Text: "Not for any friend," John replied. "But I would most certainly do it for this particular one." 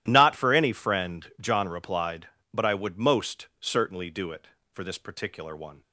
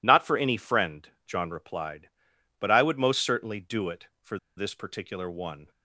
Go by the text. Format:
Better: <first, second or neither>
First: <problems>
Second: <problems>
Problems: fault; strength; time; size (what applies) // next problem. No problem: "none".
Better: first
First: none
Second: pauses between "for" and "this"; slight; at 4.3 s; 0.20 s long